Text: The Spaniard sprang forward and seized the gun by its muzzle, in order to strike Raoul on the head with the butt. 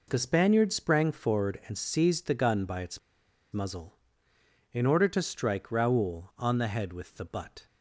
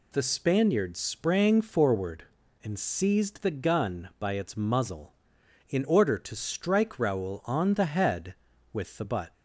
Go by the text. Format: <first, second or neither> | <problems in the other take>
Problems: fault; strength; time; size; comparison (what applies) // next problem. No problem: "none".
second | pauses between "its" and "muzzle"; noticeable; at 2.9 s; 0.53 s long